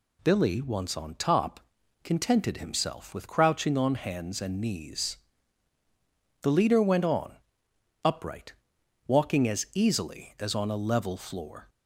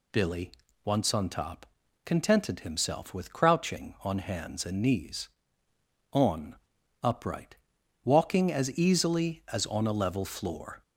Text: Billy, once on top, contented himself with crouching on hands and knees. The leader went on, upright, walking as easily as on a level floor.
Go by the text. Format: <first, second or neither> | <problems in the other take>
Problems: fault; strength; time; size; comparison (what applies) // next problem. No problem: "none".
first | skips "The leader went"; at 5.7 s